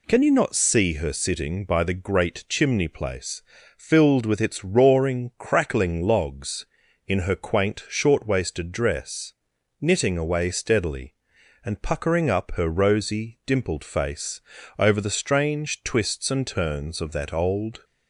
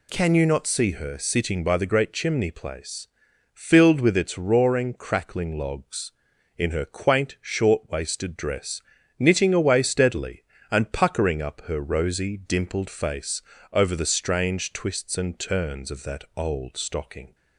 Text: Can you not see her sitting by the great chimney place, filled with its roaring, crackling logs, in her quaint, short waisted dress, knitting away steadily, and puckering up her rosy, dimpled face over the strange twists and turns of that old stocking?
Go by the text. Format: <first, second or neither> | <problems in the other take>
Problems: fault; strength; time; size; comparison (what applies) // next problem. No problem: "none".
second | pauses between "face" and "over"; slight; at 14.4 s; 0.36 s long; slight in the second // stops before "stocking"; at 17.8 s